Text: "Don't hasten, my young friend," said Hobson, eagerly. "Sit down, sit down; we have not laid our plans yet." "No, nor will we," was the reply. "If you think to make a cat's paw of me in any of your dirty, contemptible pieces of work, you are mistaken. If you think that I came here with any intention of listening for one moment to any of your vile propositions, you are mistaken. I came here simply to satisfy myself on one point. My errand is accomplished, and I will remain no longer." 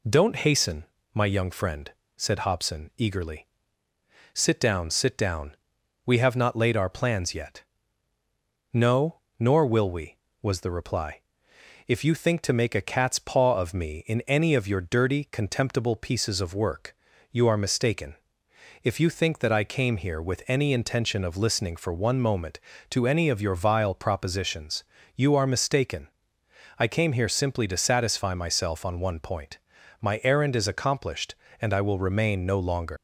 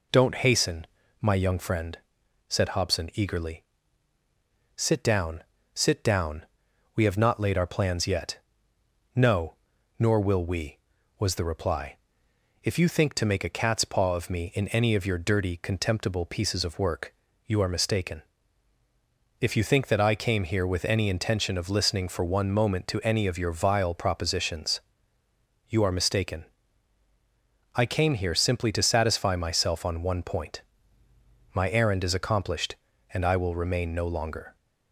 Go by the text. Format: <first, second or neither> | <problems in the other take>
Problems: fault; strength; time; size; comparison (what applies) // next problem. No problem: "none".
second | leaves "longer" unfinished; at 32.9 s; 105 ms